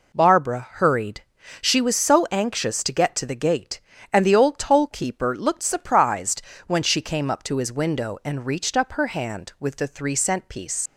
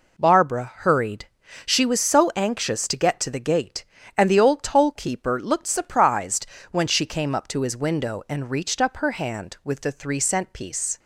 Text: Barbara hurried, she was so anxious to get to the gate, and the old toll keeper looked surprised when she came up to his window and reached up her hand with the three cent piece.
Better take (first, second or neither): second